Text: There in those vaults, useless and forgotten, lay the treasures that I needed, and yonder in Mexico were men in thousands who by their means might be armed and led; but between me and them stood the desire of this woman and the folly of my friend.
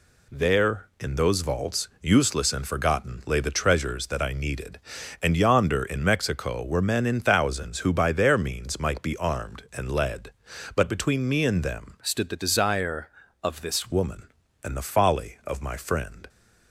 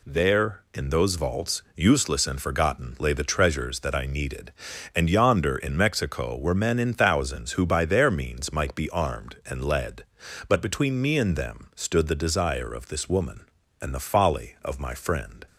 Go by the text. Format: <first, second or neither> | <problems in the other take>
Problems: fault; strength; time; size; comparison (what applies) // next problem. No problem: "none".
second | changes voice from "stood" to "this"; from 12.0 to 13.9 s; 1.9 s long